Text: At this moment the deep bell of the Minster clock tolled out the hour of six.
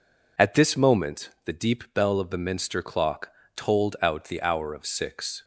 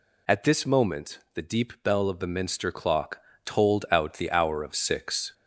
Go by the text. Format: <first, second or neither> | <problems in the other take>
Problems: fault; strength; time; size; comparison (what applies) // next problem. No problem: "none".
first | gets louder; slight; throughout; 2.5 dB // pauses between "clock" and "tolled"; slight; at 3.2 s; 0.22 s long; slight in the first